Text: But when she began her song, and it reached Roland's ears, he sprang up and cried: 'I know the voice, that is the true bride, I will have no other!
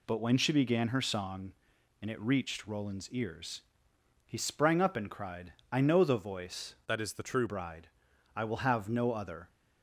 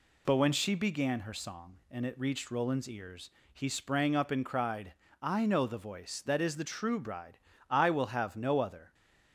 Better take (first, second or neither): second